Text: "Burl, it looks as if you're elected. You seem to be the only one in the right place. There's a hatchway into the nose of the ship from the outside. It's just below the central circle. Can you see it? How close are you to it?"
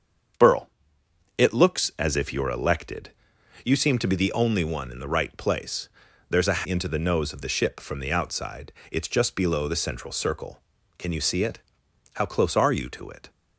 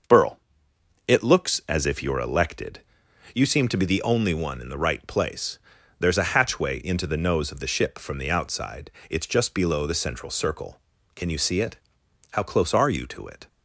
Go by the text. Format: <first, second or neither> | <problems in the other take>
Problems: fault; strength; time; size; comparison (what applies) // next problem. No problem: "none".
second | starts louder than the rest; strong; until 2.1 s; 7.5 dB; noticeable in the second // skips "hatchway"; at 6.6 s